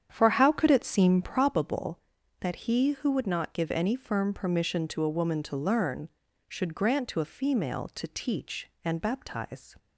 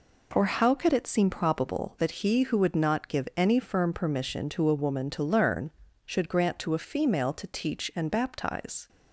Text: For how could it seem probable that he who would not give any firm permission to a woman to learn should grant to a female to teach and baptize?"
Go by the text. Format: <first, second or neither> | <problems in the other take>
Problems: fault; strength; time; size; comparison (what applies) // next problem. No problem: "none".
second | starts louder than the rest; strong; until 1.5 s; 8.5 dB